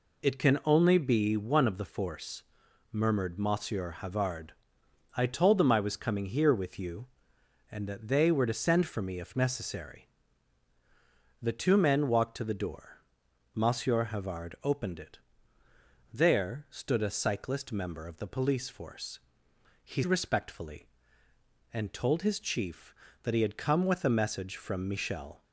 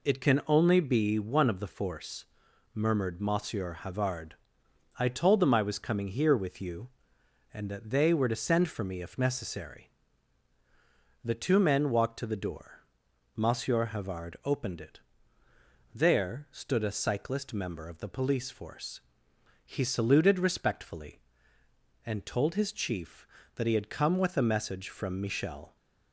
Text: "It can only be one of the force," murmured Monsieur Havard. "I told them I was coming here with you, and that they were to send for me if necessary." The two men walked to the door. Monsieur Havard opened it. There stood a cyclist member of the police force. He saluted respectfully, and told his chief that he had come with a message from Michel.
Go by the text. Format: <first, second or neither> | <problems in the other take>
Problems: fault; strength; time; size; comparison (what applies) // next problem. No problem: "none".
second | skips "saluted"; at 20.0 s